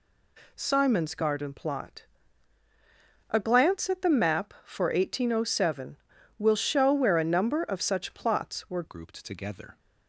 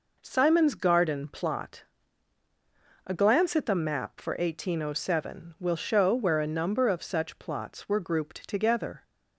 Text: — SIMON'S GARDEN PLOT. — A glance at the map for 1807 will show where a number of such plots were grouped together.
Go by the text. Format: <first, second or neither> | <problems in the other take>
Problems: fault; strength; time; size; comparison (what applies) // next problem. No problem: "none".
second | changes voice at "grouped"; from 8.8 s on; 0.9 s long